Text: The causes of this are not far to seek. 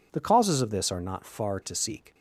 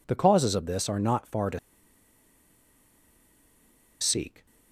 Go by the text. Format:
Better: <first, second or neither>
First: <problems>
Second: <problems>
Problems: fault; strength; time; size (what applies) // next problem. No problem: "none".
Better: first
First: none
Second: pauses between "to" and "seek"; strong; at 1.5 s; 2.4 s long